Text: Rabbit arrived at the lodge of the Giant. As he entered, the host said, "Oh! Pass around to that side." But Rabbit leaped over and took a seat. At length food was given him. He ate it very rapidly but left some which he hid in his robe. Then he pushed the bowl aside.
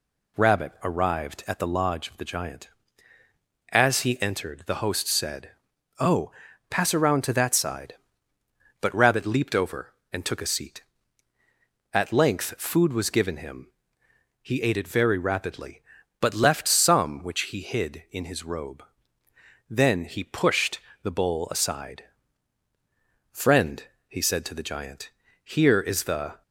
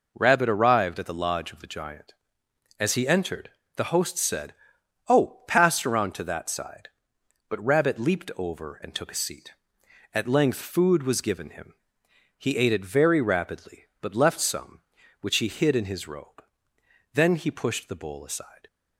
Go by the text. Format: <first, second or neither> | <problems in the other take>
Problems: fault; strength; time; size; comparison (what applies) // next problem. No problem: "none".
second | pauses between "pushed" and "the"; slight; at 20.7 s; 0.24 s long // goes on to say "Friend he said to the Giant here is the"; strong; from 23.3 s on; 3.1 s long